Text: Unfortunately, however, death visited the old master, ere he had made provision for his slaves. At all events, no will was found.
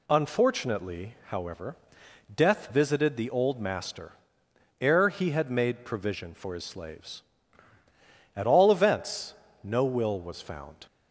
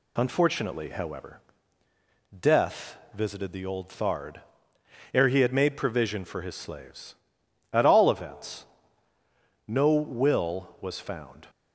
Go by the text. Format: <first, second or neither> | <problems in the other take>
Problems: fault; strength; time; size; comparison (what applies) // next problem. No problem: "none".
first | pauses between "death" and "visited"; slight; at 2.9 s; 0.18 s long // says "thard" for "master"; at 3.8 s